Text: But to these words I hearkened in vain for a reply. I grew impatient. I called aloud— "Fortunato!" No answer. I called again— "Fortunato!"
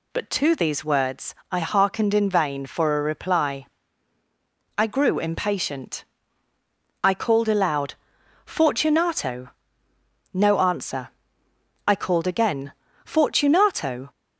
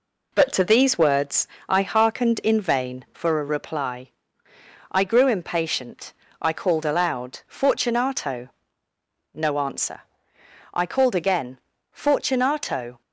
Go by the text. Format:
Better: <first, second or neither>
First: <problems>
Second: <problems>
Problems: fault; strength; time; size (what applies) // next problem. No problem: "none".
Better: neither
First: pauses between "words" and "I"; slight; at 1.3 s; 0.16 s long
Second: pauses between "words" and "I"; slight; at 1.4 s; 0.22 s long